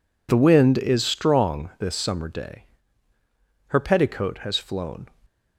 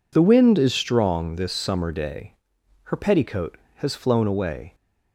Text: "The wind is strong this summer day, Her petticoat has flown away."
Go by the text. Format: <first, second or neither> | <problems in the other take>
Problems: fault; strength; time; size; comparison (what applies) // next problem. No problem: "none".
second | stops before "away"; at 5.2 s